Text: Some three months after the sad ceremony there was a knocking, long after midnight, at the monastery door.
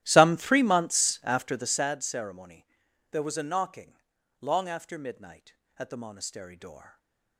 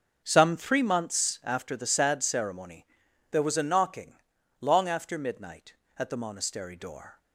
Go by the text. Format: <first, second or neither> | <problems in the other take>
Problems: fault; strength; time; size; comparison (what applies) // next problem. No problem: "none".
second | starts louder than the rest; strong; until 1.8 s; 13 dB // pauses between "ceremony" and "there"; noticeable; at 2.6 s; 0.46 s long; noticeable in the second // stays silent after the last word; slight; from 6.8 s on; 0.5 s long